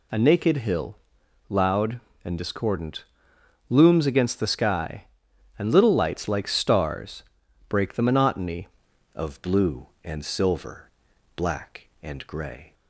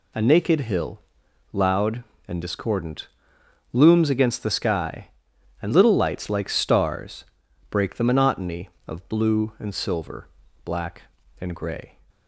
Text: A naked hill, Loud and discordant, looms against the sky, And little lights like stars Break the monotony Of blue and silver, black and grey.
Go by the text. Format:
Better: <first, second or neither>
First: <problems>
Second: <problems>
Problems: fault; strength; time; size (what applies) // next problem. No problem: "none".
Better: second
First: pauses between "stars" and "Break"; noticeable; at 7.2 s; 0.46 s long // changes voice at "Of"; from 9.1 s on; 3.6 s long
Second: pauses between "stars" and "Break"; noticeable; at 7.2 s; 0.46 s long